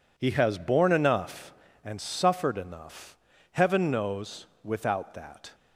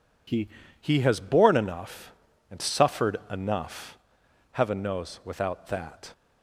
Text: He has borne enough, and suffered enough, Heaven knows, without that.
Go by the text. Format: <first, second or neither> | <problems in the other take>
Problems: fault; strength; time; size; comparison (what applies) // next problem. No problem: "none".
first | says "He" twice; at 0.7 s